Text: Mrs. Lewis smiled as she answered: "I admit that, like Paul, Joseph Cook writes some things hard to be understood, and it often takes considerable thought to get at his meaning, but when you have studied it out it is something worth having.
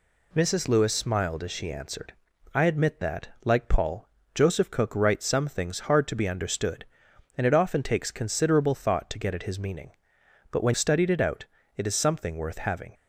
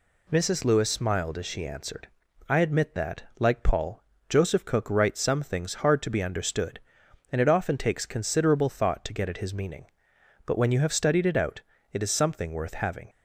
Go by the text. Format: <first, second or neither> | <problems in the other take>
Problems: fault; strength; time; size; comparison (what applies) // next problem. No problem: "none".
second | skips "you have"; at 10.7 s // pauses between "out" and "it"; slight; at 11.4 s; 0.32 s long; slight in the second